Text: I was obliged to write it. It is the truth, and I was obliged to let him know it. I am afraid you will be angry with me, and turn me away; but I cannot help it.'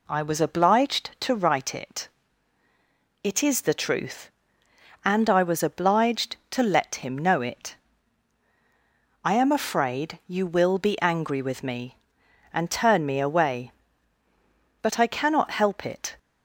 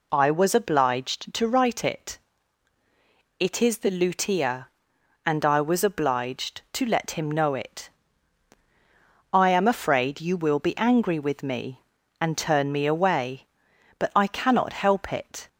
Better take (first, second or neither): first